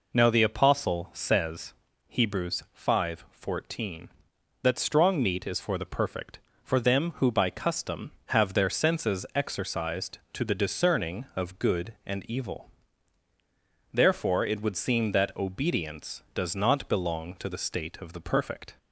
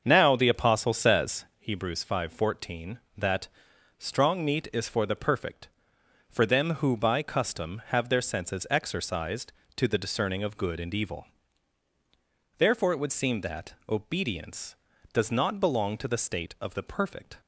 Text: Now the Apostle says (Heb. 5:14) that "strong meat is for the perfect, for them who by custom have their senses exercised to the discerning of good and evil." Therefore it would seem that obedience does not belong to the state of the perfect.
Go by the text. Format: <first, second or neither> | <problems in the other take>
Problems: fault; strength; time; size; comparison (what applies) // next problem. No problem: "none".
first | starts louder than the rest; until 1.8 s; 6.5 dB // pauses between "that" and "strong"; noticeable; at 3.4 s; 0.50 s long // pauses between "that" and "obedience"; slight; at 13.7 s; 0.16 s long